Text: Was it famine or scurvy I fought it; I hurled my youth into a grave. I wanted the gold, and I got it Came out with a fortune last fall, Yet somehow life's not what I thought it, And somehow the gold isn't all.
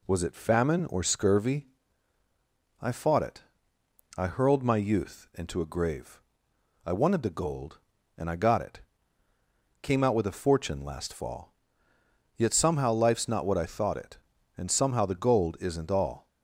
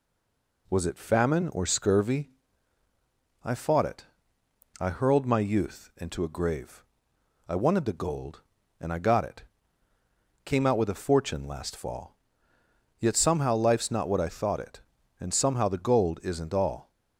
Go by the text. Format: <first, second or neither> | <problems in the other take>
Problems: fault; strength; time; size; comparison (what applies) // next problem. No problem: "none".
first | stays silent before the first word; slight; until 0.6 s; 0.6 s long // pauses between "scurvy" and "I"; at 2.3 s; 1.1 s long; also in the first // pauses between "it" and "Came"; at 9.4 s; 1.0 s long; also in the first